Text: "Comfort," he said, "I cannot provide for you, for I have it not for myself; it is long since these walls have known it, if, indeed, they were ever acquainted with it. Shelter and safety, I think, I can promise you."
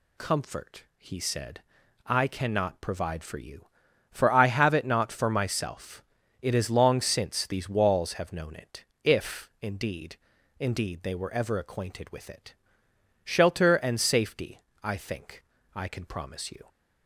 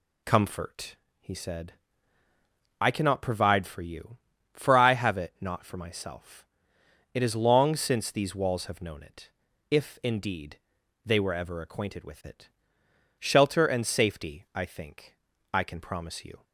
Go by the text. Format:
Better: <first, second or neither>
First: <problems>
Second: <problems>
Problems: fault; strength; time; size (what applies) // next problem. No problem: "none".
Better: second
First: says "indeed" twice; at 10.5 s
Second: none